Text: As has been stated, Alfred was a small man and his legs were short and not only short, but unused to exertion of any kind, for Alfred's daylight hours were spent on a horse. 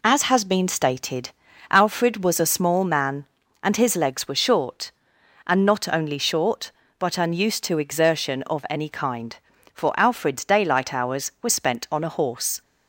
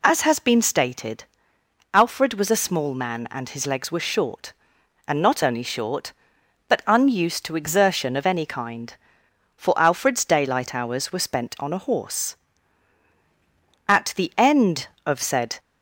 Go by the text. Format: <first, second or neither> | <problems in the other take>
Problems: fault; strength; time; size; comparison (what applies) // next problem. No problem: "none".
first | goes on to say "At the end of said"; strong; from 13.8 s on; 1.7 s long